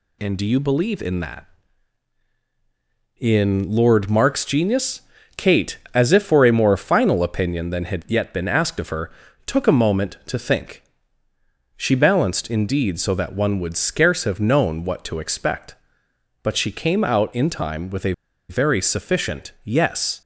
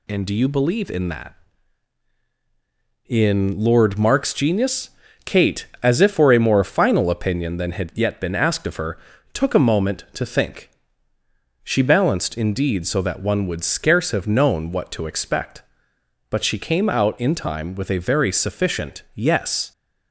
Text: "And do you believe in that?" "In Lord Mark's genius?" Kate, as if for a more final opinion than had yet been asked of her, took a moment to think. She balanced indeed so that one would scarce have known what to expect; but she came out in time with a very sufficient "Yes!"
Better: second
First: pauses between "a" and "very"; at 18.1 s; 0.36 s long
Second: none

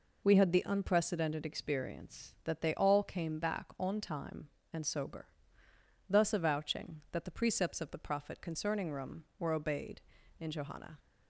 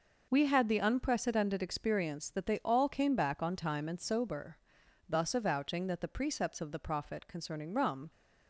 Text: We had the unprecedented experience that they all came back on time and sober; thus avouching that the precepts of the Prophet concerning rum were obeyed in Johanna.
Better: first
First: none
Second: stops before "were obeyed in Johanna"; at 8.1 s

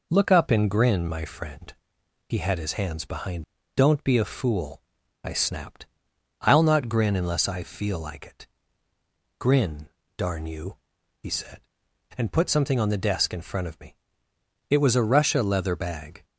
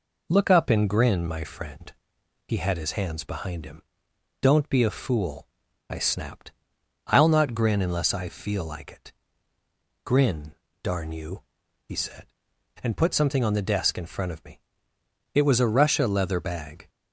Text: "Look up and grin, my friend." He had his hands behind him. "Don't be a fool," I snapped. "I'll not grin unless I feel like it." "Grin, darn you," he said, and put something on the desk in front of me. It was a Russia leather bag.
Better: second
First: skips "him"; at 3.6 s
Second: none

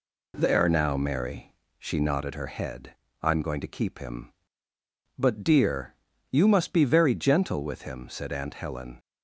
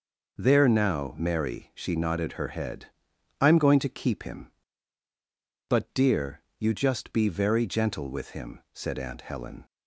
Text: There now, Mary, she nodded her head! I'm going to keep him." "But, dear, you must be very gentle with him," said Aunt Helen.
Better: first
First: none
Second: says "just" for "must"; at 6.7 s

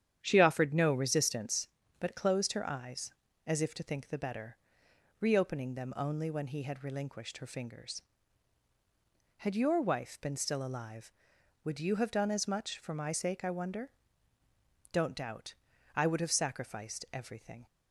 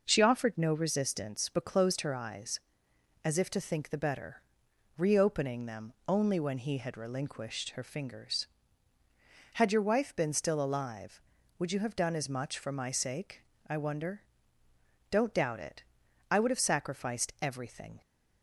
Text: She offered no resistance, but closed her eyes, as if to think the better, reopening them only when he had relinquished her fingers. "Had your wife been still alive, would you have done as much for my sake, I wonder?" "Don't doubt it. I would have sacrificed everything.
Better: second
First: starts louder than the rest; strong; until 1.2 s; 9.5 dB // skips "it"; at 15.7 s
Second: none

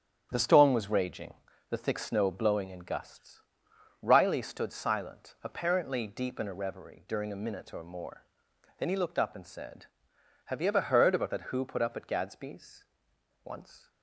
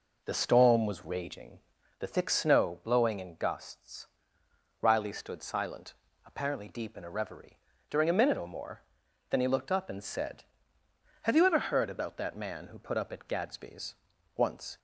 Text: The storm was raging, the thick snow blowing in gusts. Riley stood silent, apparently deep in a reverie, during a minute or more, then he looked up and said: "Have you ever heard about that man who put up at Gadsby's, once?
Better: second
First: starts louder than the rest; strong; until 1.3 s; 9 dB // skips "man"; at 11.5 s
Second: none

